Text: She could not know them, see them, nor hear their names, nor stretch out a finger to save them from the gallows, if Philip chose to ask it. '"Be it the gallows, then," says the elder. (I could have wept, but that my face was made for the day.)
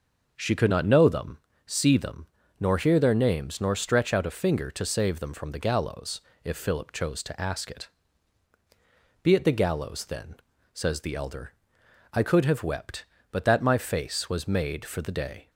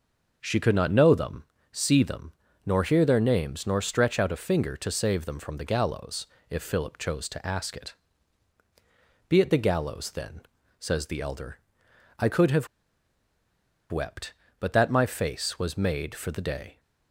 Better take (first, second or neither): first